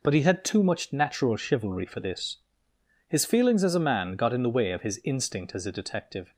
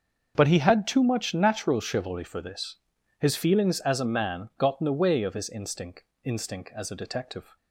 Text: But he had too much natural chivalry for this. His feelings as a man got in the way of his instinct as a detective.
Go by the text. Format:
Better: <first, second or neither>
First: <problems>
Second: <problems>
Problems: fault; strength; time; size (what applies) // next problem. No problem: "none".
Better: first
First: none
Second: starts louder than the rest; until 1.3 s; 6.5 dB // says "instinct" twice; at 6.2 s